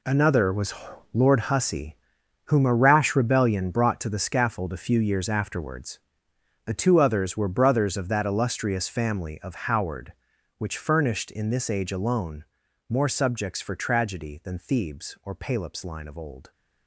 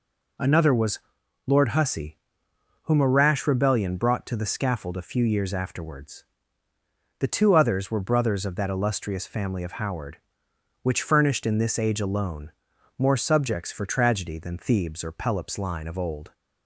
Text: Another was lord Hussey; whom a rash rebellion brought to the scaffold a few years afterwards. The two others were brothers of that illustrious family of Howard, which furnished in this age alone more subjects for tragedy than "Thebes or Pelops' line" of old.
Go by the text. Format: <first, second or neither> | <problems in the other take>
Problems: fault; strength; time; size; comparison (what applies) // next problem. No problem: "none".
second | gets quieter; strong; throughout; 13 dB // pauses between "was" and "lord"; at 0.7 s; 0.40 s long; noticeable in the second // pauses between "alone" and "more"; at 12.4 s; 0.44 s long; noticeable in the second